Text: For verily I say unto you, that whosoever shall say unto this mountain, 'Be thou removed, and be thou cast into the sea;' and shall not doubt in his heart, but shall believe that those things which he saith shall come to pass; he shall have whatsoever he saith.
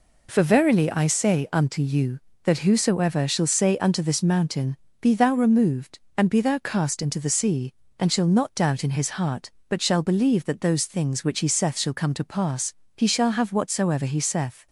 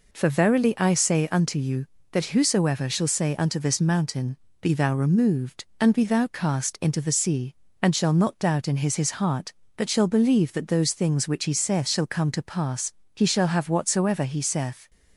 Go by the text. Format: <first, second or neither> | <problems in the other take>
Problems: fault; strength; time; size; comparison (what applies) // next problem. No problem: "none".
first | says "his" twice; at 8.9 s